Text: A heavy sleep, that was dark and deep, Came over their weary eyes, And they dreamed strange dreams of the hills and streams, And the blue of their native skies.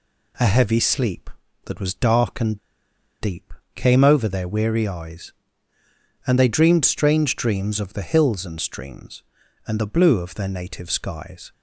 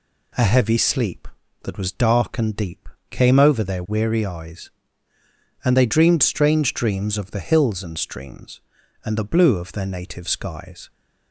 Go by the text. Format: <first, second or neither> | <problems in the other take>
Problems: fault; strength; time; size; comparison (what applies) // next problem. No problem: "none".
second | pauses between "and" and "deep"; noticeable; at 2.5 s; 0.63 s long